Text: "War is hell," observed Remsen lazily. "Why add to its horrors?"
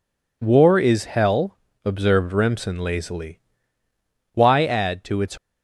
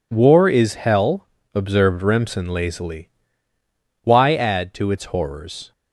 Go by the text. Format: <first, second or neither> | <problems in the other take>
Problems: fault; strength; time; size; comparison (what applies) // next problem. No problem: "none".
second | stops before "horrors"; at 5.3 s